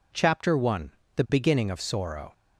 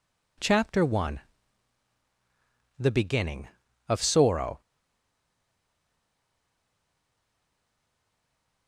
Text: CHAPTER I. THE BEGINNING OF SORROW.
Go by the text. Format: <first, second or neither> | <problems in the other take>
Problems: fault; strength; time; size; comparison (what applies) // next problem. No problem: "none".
first | stays silent after the last word; strong; from 4.6 s on; 4.0 s long